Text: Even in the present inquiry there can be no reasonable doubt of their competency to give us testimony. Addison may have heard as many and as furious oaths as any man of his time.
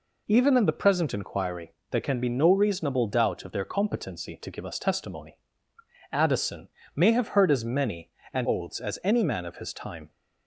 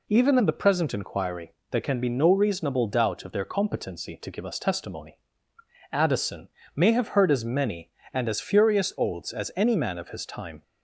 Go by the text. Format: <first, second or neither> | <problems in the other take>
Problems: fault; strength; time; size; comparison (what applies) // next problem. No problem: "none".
second | pauses between "inquiry" and "there"; slight; at 1.7 s; 0.18 s long; slight in the second // pauses between "Addison" and "may"; slight; at 6.6 s; 0.28 s long; slight in the second // skips "as furious"; at 8.4 s